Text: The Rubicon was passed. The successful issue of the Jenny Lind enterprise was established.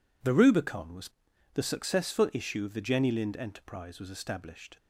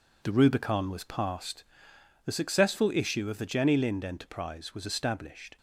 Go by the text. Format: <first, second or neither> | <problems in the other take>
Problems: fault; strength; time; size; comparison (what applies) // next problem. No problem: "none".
second | skips "passed"; at 1.3 s